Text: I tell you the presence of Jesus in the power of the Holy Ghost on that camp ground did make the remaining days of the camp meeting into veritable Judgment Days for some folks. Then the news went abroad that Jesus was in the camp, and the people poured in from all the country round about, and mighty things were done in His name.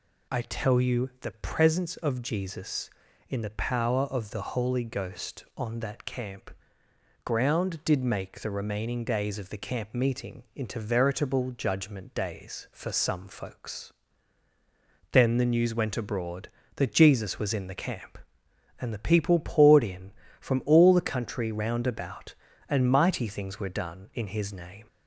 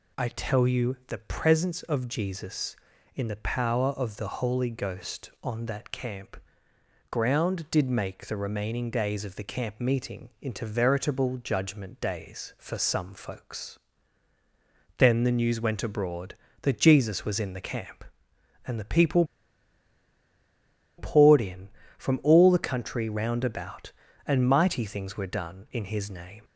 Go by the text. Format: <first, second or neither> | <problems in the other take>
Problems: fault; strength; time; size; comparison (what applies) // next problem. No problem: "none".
first | pauses between "camp" and "ground"; noticeable; at 6.3 s; 0.72 s long; noticeable in the first // pauses between "people" and "poured"; strong; at 19.2 s; 1.7 s long